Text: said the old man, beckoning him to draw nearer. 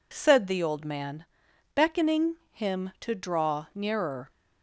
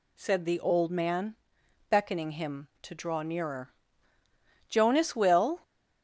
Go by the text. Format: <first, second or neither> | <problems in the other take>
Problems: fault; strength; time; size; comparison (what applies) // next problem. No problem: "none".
first | goes on to say "Jonas will"; noticeable; from 4.7 s on; 0.90 s long